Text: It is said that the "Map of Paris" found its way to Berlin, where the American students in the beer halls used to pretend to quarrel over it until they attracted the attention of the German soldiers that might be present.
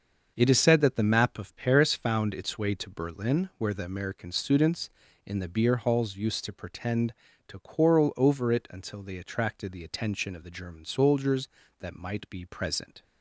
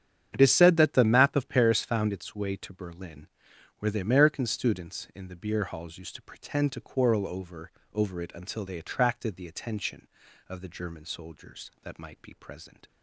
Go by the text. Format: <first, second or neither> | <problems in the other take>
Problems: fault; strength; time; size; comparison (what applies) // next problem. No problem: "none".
first | starts louder than the rest; strong; until 1.3 s; 8.5 dB; also in the first // says "over" twice; at 7.9 s